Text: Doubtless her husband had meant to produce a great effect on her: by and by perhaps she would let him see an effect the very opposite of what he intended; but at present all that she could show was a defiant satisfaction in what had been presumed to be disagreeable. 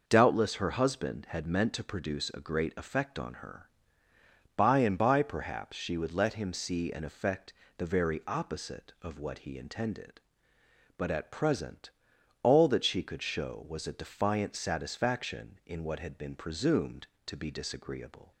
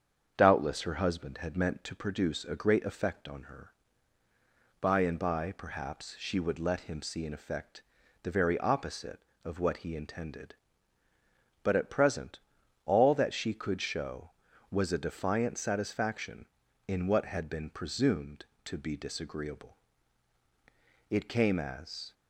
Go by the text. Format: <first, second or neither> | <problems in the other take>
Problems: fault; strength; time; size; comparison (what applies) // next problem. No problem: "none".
first | starts louder than the rest; strong; until 1.3 s; 7 dB // pauses between "effect" and "the"; at 7.8 s; 0.40 s long; slight in the first // pauses between "present" and "all"; noticeable; at 12.3 s; 0.46 s long; noticeable in the first // goes on to say "It came as"; noticeable; from 21.1 s on; 1.0 s long